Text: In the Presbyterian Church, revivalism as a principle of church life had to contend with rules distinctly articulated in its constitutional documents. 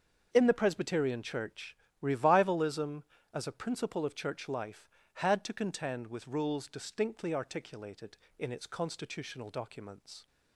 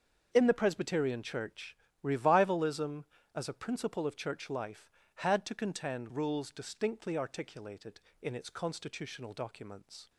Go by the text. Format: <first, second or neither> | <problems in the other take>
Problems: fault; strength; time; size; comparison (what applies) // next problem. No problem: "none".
first | starts louder than the rest; until 1.3 s; 6.5 dB; also in the first // skips "with"; at 6.0 s